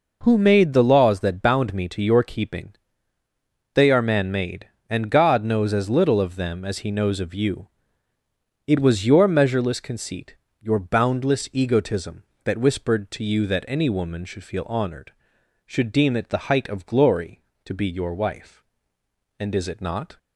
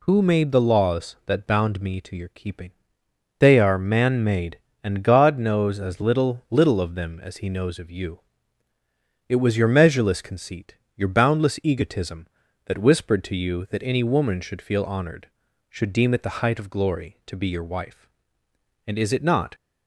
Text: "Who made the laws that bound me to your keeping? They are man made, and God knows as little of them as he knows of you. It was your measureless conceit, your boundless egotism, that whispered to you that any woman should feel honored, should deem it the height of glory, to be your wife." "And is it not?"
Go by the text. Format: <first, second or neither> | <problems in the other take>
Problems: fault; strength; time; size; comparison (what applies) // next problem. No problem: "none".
first | says "little" twice; at 6.5 s